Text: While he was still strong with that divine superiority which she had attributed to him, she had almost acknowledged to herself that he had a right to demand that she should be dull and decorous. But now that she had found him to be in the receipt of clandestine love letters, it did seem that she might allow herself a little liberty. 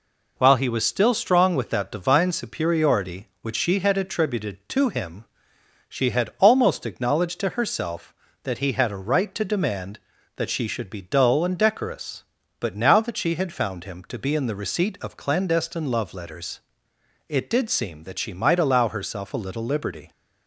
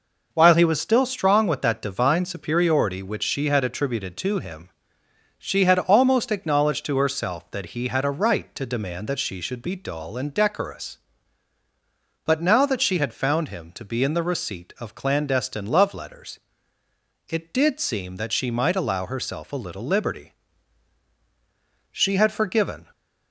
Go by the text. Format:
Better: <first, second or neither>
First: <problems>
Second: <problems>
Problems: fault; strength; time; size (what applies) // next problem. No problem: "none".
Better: first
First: none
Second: goes on to say "She had forgiven"; noticeable; from 21.8 s on; 1.0 s long